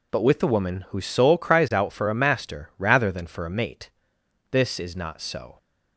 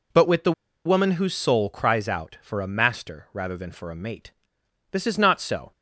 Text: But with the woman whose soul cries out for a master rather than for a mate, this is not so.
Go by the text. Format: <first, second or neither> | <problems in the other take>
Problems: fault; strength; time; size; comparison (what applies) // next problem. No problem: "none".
first | pauses between "the" and "woman"; slight; at 0.5 s; 0.32 s long